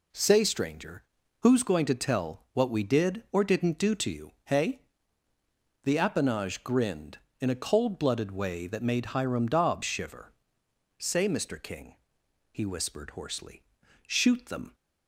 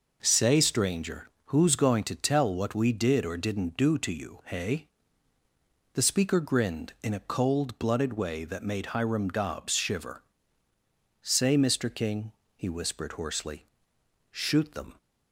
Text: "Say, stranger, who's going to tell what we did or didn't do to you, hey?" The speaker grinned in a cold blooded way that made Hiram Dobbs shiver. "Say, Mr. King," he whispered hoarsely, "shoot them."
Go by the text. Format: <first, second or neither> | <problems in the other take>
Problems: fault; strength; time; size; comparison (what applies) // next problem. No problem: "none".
second | says "appanage" for "speaker"; at 5.9 s